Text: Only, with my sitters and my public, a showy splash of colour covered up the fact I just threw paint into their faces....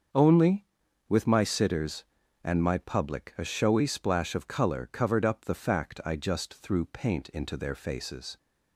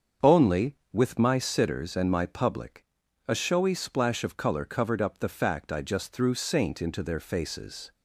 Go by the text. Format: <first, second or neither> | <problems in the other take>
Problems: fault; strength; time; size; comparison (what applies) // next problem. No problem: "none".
first | starts louder than the rest; strong; until 1.3 s; 7 dB; also in the first // says "saint" for "paint"; at 6.3 s